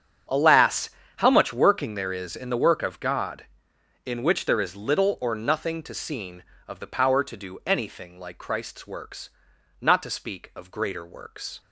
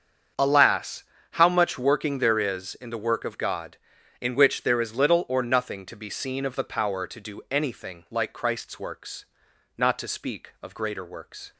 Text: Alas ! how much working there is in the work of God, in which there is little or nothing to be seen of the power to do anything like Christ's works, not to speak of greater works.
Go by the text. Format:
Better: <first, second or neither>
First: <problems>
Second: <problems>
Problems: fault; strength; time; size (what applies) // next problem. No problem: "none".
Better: second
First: starts louder than the rest; strong; until 1.5 s; 7.5 dB // skips "be"; at 5.9 s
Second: starts louder than the rest; strong; until 1.6 s; 7.5 dB